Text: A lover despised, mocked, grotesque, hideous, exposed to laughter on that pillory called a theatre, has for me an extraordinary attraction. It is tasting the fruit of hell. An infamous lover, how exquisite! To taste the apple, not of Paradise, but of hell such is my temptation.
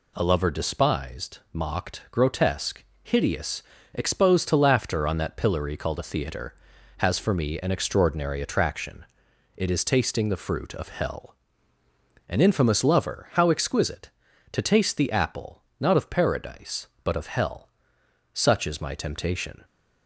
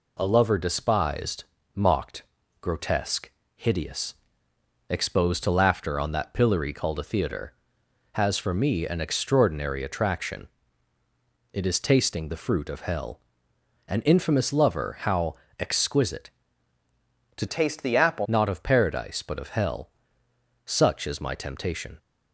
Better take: first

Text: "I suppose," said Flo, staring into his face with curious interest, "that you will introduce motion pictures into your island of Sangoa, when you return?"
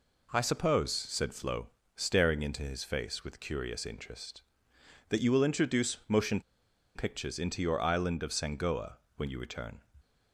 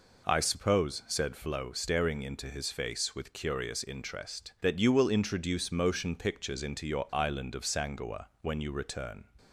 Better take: second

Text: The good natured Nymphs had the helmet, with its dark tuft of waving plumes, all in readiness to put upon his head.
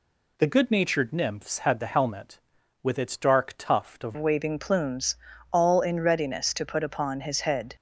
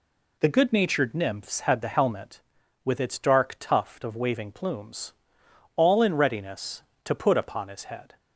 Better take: second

